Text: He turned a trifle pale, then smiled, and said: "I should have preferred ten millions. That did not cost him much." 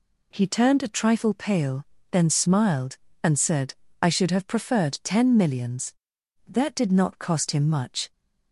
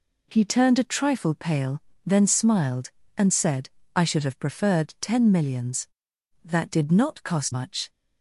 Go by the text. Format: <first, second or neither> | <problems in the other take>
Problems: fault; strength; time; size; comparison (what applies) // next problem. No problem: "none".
first | skips "him"; at 7.5 s